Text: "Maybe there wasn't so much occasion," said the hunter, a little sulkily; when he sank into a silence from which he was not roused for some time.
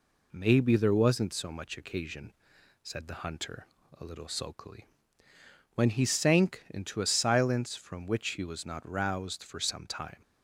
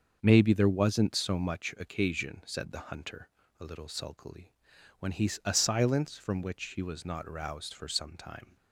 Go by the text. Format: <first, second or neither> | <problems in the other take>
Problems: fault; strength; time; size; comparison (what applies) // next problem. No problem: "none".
first | starts louder than the rest; until 1.2 s; 6.5 dB // skips "sank into"; at 5.3 s